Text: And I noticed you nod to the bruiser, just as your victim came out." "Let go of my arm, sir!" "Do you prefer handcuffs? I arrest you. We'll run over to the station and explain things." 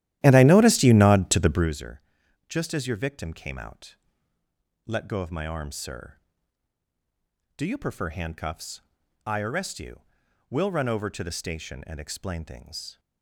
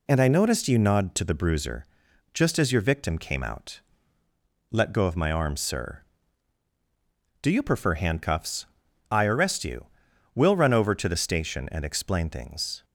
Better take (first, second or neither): second